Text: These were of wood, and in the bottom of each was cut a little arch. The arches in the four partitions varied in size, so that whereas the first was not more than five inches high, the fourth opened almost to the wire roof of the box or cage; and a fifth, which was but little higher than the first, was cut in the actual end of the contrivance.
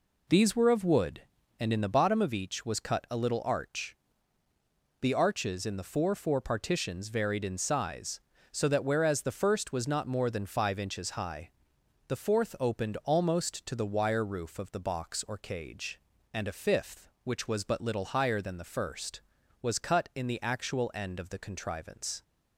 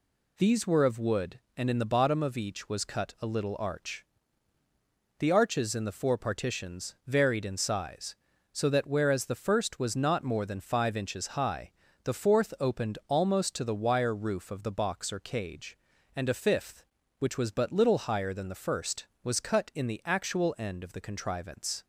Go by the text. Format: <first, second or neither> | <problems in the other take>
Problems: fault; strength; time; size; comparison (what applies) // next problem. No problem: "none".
second | says "four" twice; at 6.1 s